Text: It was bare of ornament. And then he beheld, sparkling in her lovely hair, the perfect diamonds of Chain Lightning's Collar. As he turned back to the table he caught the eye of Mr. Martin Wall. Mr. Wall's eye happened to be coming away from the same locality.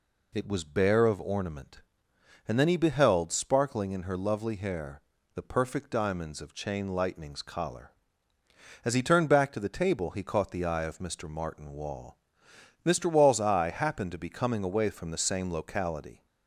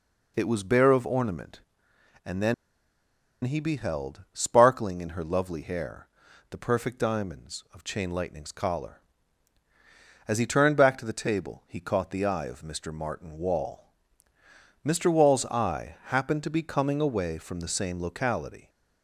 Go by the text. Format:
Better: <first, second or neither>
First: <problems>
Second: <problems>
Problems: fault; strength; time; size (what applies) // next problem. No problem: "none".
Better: first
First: none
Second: pauses between "then" and "he"; noticeable; at 2.5 s; 0.90 s long